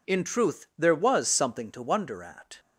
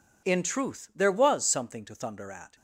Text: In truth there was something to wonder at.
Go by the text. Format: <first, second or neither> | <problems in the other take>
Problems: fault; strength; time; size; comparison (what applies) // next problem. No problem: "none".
first | says "thunder" for "wonder"; at 1.9 s